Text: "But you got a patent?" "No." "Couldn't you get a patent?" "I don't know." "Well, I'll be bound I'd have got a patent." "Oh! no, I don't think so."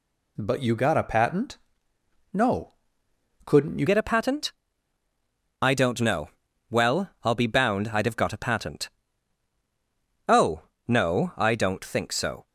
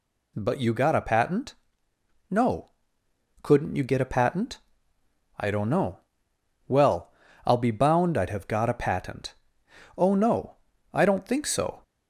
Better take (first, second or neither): second